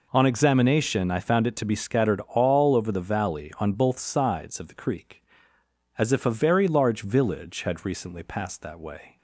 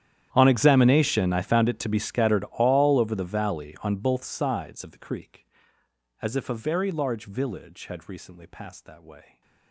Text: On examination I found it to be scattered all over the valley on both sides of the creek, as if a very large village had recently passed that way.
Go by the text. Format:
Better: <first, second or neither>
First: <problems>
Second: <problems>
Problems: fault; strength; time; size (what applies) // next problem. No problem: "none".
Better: first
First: none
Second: gets quieter; strong; throughout; 24 dB